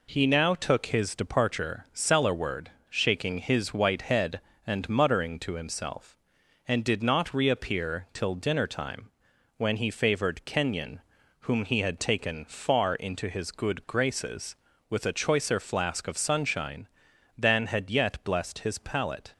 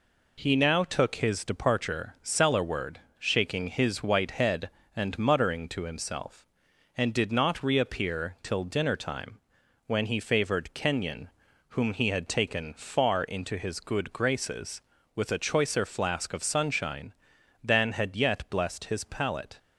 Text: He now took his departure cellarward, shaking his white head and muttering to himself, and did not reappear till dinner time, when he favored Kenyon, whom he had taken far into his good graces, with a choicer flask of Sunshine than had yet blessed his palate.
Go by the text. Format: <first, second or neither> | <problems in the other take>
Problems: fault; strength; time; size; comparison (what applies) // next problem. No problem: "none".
neither | none